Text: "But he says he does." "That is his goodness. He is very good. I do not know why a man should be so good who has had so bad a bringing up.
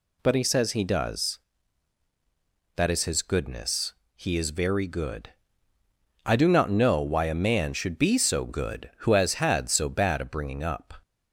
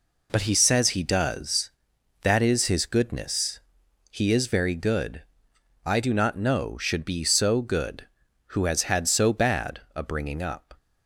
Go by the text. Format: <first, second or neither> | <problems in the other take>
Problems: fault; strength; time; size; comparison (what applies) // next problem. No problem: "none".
first | skips "why a man"; at 6.7 s